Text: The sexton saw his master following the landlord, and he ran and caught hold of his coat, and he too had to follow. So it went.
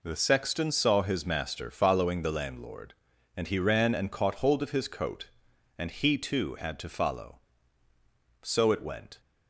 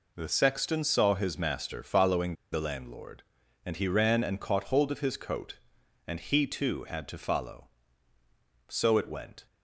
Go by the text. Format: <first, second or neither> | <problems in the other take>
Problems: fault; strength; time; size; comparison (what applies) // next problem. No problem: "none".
first | pauses between "following" and "the"; slight; at 2.3 s; 0.18 s long